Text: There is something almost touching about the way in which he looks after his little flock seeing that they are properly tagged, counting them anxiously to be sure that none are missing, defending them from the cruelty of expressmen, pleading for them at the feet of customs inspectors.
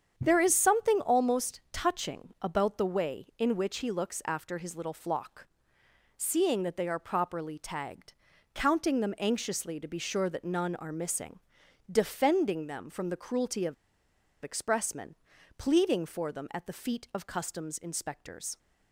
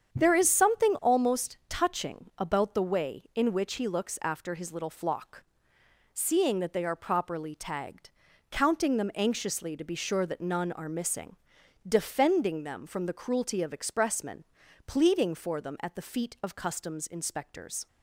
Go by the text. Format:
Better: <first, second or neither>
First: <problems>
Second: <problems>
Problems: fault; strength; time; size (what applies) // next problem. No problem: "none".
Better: second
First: starts louder than the rest; strong; until 1.2 s; 8 dB // pauses between "flock" and "seeing"; noticeable; at 5.4 s; 0.72 s long // pauses between "of" and "expressmen"; noticeable; at 13.7 s; 0.69 s long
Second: starts louder than the rest; strong; until 1.2 s; 8 dB // pauses between "flock" and "seeing"; noticeable; at 5.4 s; 0.72 s long